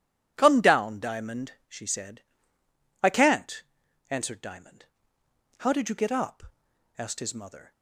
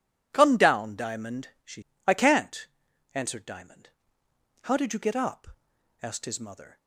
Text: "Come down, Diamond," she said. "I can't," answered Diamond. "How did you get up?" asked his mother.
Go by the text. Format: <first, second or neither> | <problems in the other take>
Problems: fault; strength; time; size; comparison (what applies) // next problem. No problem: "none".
first | skips "said"; at 1.9 s